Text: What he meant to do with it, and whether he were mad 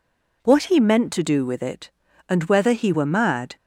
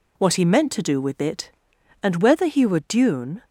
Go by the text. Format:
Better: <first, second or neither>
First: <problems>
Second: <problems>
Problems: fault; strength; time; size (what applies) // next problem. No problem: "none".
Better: first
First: none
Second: says "dune" for "mad"; at 2.7 s